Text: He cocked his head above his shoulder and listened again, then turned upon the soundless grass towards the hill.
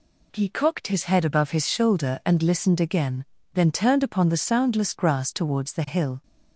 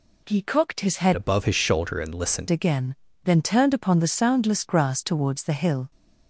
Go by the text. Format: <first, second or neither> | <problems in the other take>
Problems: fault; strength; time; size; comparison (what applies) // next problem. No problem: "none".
first | changes voice from "above" to "listened"; from 1.1 to 2.4 s; 1.3 s long